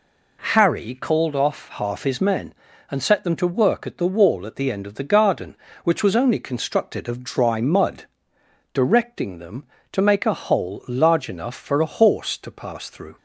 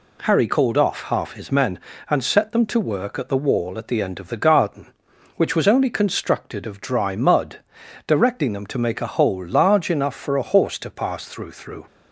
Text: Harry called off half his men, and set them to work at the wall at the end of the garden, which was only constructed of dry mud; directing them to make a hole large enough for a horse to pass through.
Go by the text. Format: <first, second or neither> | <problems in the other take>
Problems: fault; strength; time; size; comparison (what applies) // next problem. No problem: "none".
first | says "through" twice; at 11.5 s